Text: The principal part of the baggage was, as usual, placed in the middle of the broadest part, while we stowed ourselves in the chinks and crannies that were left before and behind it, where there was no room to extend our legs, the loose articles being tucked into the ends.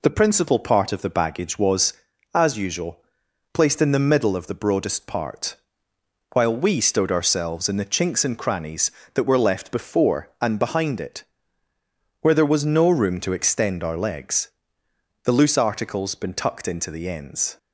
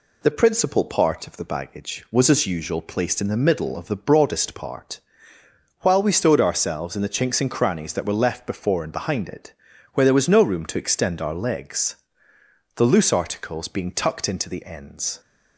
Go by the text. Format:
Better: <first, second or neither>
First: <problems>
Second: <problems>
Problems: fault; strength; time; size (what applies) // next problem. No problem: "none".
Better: second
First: says "been" for "being"; at 16.1 s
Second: none